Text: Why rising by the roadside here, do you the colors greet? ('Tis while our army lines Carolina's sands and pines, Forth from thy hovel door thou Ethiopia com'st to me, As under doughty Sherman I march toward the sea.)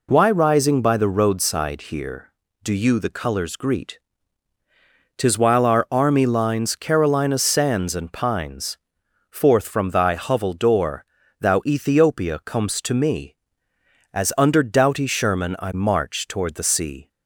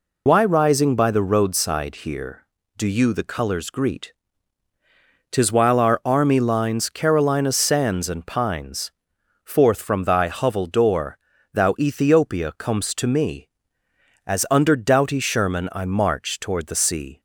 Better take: first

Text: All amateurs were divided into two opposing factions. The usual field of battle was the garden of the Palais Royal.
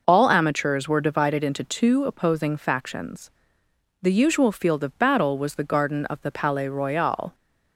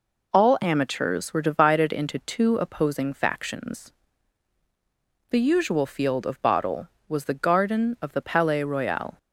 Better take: first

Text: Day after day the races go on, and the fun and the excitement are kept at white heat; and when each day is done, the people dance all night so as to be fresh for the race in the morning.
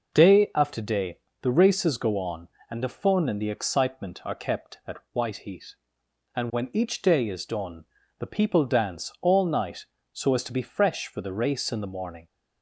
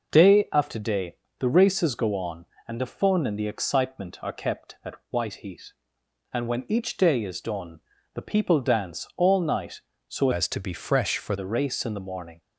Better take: first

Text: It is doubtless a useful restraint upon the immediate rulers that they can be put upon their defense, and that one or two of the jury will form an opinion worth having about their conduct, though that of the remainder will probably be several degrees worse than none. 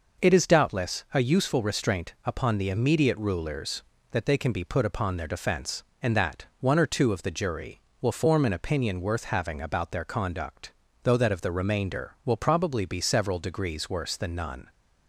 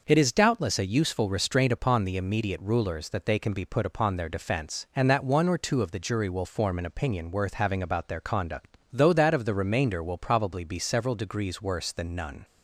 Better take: neither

